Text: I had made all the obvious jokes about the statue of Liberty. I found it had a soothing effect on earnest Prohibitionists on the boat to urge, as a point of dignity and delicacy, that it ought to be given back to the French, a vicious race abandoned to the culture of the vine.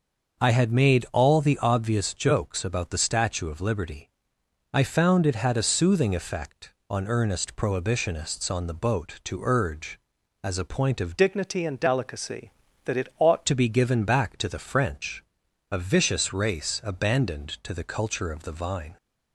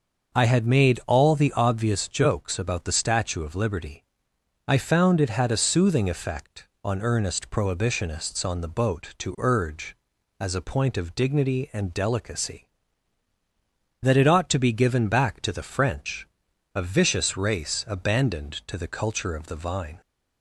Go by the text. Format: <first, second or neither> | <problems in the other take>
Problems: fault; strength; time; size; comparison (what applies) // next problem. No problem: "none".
second | starts louder than the rest; until 1.4 s; 6.5 dB; also in the second // changes voice from "dignity" to "ought"; from 11.1 to 13.4 s; 2.3 s long